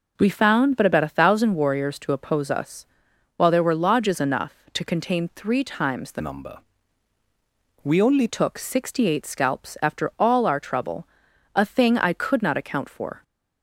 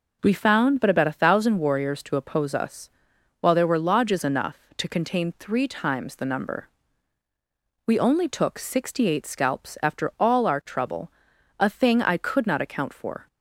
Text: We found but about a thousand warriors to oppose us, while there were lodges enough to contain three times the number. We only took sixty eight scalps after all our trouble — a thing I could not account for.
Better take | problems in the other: second | changes voice from "number" to "only"; from 6.1 to 8.2 s; 2.1 s long

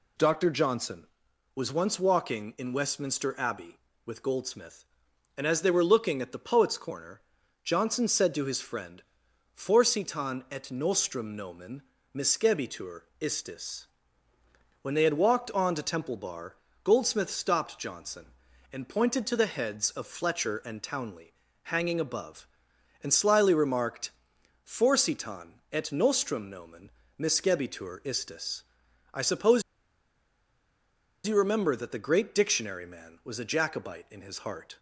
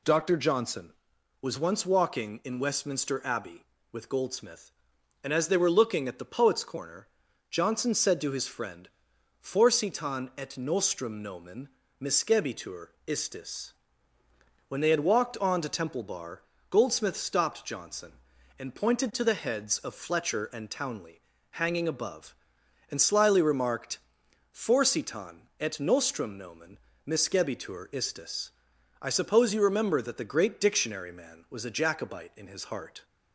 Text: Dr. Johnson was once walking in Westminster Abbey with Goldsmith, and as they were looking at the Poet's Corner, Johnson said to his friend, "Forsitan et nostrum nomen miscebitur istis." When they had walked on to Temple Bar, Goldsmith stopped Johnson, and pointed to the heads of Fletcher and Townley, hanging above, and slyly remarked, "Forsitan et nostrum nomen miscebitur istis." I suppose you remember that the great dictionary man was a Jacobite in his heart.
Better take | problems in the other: second | pauses between "nomen" and "miscebitur"; slight; at 11.8 s; 0.32 s long; slight in the second // pauses between "miscebitur" and "istis"; slight; at 13.0 s; 0.18 s long; slight in the second // pauses between "nomen" and "miscebitur"; slight; at 26.8 s; 0.30 s long; slight in the second // pauses between "suppose" and "you"; strong; at 29.6 s; 1.6 s long

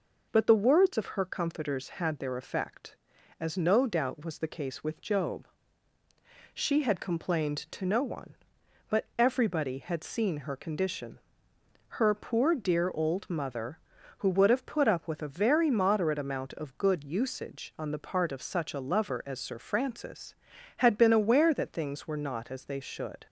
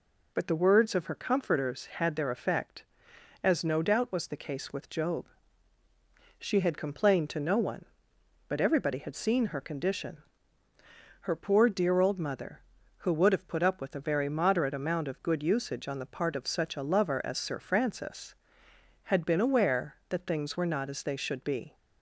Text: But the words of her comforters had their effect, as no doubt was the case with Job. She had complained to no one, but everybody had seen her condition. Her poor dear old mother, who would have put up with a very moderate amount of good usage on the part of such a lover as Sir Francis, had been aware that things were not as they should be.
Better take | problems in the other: second | stops before "be"; at 23.2 s

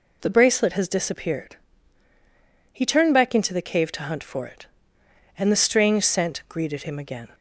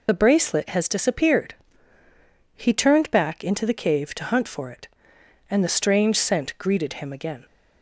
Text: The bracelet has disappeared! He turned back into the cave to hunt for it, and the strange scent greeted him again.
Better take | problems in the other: first | loses the start of "The"; at 0.0 s; 45 ms

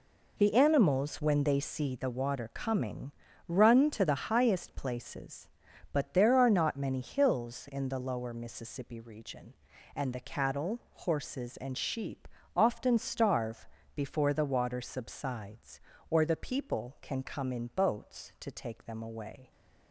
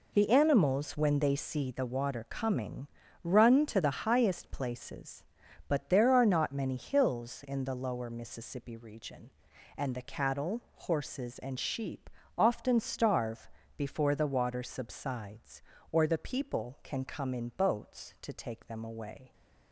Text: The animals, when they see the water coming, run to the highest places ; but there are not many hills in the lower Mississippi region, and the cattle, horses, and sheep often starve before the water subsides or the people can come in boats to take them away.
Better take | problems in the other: neither | pauses between "sheep" and "often"; slight; the same in both // pauses between "starve" and "before"; slight; the same in both

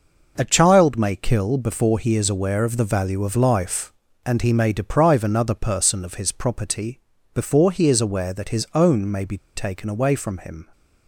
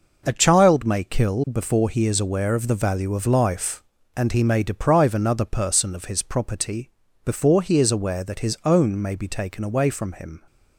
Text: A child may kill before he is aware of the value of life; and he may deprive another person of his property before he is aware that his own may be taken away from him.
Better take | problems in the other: second | pauses between "property" and "before"; slight; at 7.0 s; 0.32 s long; slight in the second // pauses between "be" and "taken"; slight; at 9.3 s; 0.16 s long

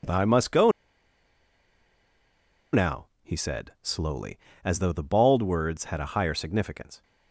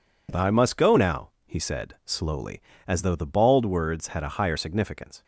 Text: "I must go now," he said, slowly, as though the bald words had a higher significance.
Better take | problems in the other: second | pauses between "go" and "now"; strong; at 0.7 s; 2.0 s long

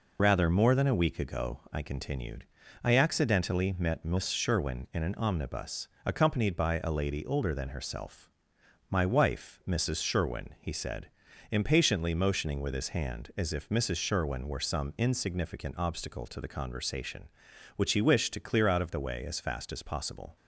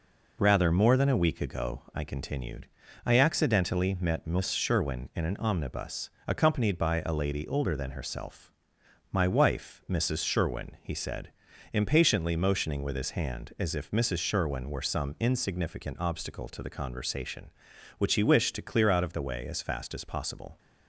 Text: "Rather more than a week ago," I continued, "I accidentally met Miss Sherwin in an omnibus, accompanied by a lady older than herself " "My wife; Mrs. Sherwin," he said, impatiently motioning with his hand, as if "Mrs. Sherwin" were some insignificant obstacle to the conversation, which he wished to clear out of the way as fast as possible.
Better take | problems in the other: second | loses the start of "Rather"; at 0.1 s; 30 ms

